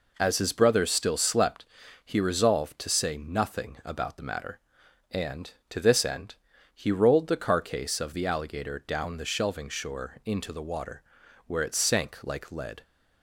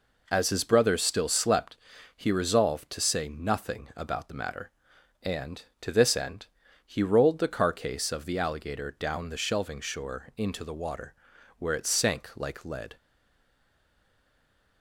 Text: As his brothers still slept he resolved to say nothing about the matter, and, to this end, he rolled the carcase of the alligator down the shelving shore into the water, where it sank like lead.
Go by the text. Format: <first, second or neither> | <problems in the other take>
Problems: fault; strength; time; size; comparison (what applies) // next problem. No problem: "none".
first | pauses between "slept" and "he"; at 1.7 s; 0.40 s long; also in the first // stays silent after the last word; noticeable; from 12.9 s on; 1.9 s long